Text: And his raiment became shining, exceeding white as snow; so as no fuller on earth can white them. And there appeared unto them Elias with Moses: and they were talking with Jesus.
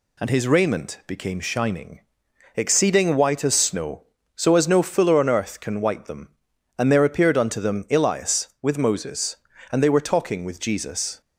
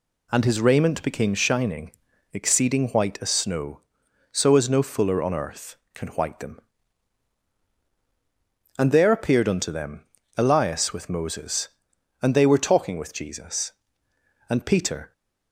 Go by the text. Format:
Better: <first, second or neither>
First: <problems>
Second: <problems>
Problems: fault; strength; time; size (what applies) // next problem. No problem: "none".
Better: first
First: none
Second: pauses between "them" and "Elias"; slight; at 10.0 s; 0.34 s long // goes on to say "And Peter"; noticeable; from 14.5 s on; 0.62 s long